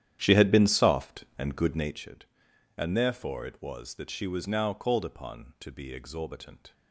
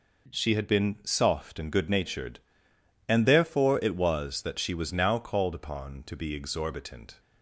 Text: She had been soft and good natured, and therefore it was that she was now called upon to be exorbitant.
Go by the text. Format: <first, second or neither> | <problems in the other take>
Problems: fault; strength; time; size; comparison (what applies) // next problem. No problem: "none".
second | starts louder than the rest; strong; until 2.1 s; 10.5 dB